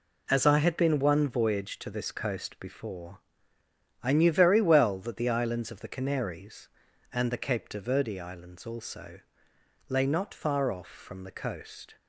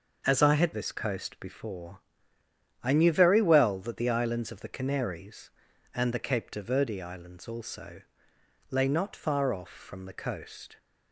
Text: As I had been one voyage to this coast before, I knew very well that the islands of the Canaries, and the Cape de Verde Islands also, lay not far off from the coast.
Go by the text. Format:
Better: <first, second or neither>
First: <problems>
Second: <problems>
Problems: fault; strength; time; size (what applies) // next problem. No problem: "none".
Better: first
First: none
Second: skips "been one voyage to"; at 0.7 s